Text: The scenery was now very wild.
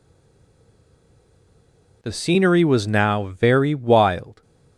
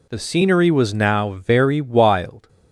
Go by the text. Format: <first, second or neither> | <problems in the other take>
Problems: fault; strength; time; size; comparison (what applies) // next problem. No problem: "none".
second | stays silent before the first word; noticeable; until 2.0 s; 2.0 s long